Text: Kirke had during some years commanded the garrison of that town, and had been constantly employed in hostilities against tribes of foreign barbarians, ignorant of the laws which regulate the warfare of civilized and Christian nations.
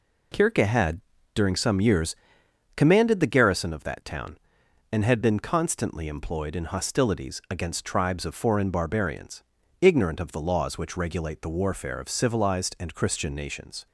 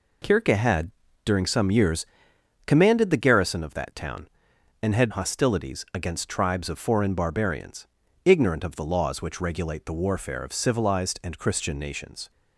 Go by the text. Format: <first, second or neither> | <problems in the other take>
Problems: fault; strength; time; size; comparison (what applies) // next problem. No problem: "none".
first | pauses between "had" and "during"; slight; at 0.9 s; 0.34 s long; slight in the first // pauses between "years" and "commanded"; noticeable; at 2.0 s; 0.60 s long; noticeable in the first // skips "been constantly employed in"; at 5.1 s